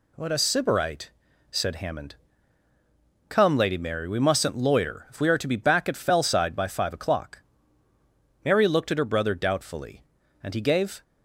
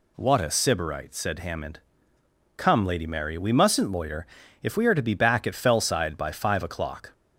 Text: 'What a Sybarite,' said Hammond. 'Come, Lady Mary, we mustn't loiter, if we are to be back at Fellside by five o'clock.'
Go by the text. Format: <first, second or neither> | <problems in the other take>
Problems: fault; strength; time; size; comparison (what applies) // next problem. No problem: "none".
second | goes on to say "Mary looked at her brother doubtfully and he gave"; strong; from 8.4 s on; 2.5 s long